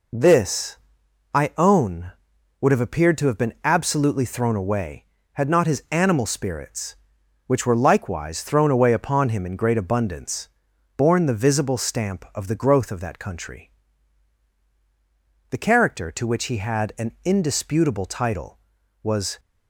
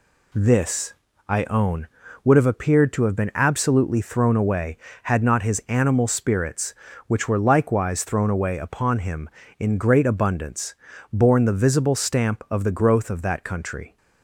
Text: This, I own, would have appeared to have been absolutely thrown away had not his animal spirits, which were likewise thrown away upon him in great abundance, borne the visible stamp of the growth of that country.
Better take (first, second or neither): second